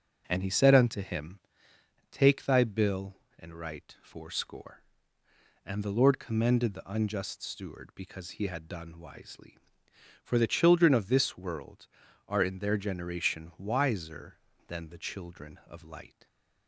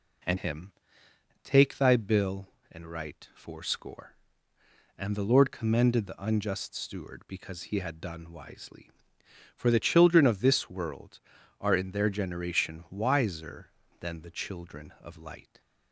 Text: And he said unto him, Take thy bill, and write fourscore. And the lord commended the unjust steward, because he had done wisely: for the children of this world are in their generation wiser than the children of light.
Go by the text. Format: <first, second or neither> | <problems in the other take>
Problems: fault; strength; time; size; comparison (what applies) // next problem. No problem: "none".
first | skips "he said unto"; at 0.3 s